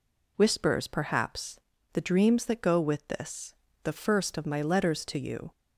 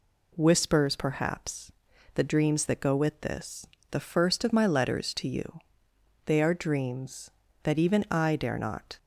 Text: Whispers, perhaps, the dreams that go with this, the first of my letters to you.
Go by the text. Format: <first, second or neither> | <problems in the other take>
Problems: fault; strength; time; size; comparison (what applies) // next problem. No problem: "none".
first | goes on to say "They are dreams that even I dare not"; strong; from 6.2 s on; 2.7 s long